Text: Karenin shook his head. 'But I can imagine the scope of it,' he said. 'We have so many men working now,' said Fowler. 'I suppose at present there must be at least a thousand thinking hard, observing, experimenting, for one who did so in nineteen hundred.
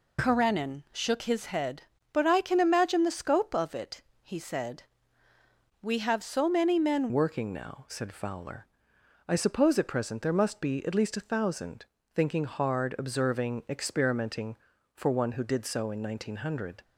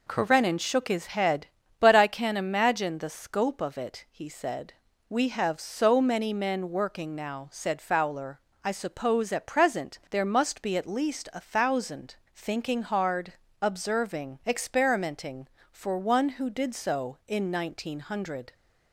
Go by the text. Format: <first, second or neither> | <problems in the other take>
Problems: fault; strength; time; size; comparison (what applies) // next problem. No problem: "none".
second | changes voice at "working"; from 7.1 s on; 9.7 s long // pauses between "thousand" and "thinking"; slight; at 11.8 s; 0.30 s long; slight in the second